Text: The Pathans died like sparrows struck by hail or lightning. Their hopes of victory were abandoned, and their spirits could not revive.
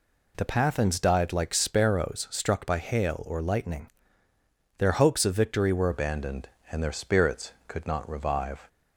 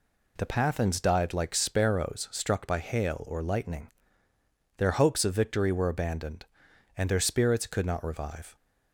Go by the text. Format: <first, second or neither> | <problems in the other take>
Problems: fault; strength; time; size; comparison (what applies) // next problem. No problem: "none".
second | changes voice at "abandoned"; from 5.9 s on; 2.7 s long